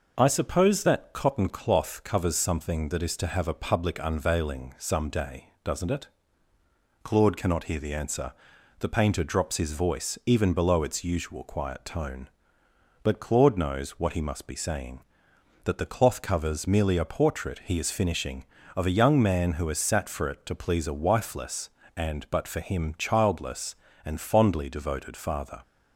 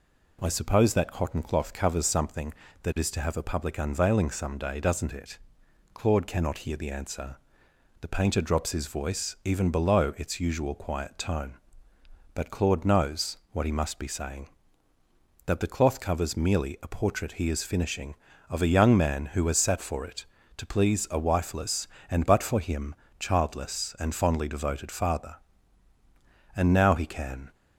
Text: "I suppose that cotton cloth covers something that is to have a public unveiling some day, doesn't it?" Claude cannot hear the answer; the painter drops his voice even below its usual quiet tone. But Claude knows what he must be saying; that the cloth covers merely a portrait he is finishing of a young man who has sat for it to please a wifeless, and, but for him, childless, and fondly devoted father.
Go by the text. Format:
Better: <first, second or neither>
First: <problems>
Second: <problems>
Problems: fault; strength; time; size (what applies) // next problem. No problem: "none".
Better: first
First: none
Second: pauses between "knows" and "what"; slight; at 13.3 s; 0.16 s long // goes on to say "And now he can"; noticeable; from 26.5 s on; 0.98 s long